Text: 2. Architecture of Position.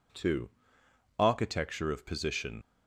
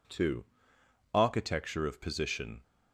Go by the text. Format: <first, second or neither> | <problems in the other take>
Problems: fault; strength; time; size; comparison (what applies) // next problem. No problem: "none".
second | leaves "Position" unfinished; at 2.6 s; 60 ms